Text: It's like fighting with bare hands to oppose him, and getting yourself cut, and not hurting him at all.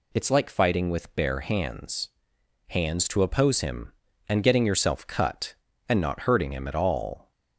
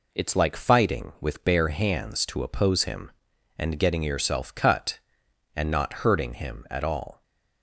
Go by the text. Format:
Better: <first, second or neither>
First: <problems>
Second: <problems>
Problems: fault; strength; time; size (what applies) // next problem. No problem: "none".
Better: second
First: says "hands" twice; at 2.7 s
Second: none